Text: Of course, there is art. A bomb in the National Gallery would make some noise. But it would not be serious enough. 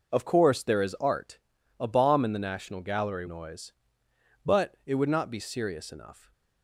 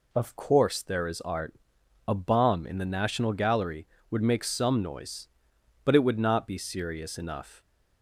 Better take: second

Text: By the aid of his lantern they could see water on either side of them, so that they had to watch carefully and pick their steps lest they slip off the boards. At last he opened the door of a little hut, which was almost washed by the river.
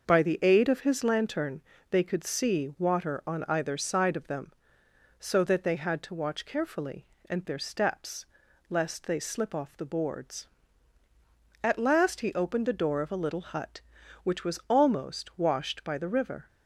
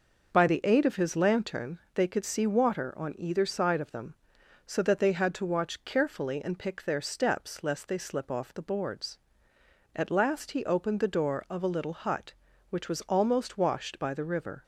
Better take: second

